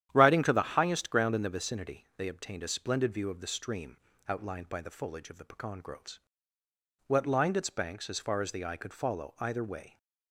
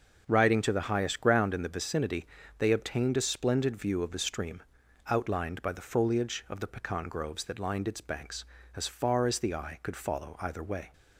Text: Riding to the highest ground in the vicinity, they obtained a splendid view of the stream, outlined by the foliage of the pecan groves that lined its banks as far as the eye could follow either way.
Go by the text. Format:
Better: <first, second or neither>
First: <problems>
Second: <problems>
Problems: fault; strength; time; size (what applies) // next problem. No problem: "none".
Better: second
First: starts louder than the rest; strong; until 1.1 s; 10.5 dB // says "what" for "that"; at 7.0 s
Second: starts louder than the rest; noticeable; until 1.2 s; 6 dB